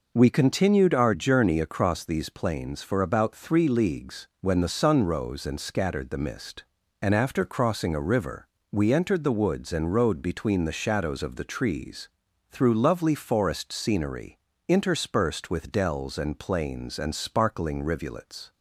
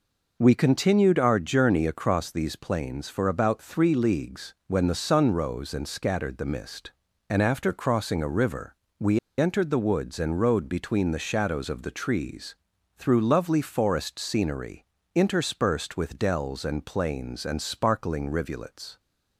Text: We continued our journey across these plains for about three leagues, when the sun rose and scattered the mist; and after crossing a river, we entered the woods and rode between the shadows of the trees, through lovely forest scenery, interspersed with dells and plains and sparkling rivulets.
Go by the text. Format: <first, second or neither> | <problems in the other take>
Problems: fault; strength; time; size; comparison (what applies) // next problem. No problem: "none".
first | pauses between "we" and "entered"; slight; at 9.1 s; 0.19 s long